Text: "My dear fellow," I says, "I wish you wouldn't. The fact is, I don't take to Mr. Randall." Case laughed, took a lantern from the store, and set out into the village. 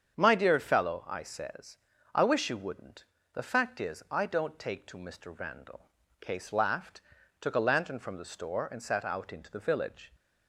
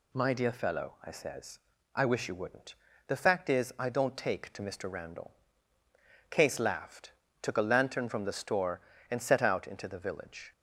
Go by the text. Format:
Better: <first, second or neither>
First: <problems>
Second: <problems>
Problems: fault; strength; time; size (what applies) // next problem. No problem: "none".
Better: second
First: starts louder than the rest; strong; until 1.2 s; 7.5 dB // says "sat" for "set"; at 8.8 s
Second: none